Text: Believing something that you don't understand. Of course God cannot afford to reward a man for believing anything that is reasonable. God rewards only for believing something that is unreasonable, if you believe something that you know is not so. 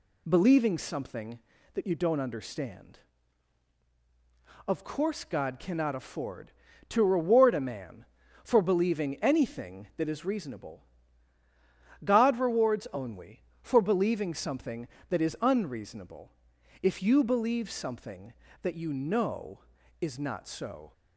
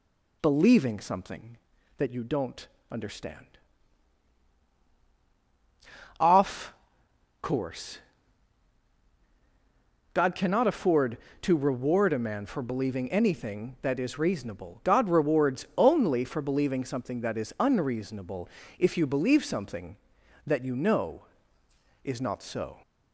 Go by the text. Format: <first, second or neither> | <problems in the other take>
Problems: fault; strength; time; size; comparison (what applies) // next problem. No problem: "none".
first | pauses between "don't" and "understand"; slight; at 2.6 s; 0.24 s long // says "Off" for "Of"; at 6.1 s // pauses between "course" and "God"; strong; at 7.9 s; 2.1 s long